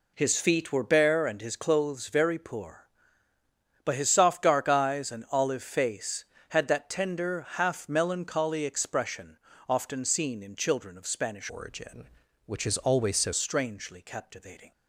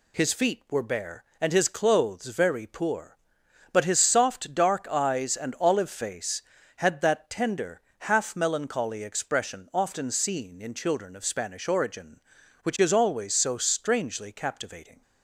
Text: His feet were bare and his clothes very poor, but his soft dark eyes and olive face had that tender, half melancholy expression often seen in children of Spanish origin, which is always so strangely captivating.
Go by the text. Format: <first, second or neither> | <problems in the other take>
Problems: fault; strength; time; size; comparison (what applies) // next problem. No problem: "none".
second | pauses between "expression" and "often"; slight; at 9.3 s; 0.30 s long // changes voice from "origin" to "so"; from 11.4 to 13.3 s; 1.9 s long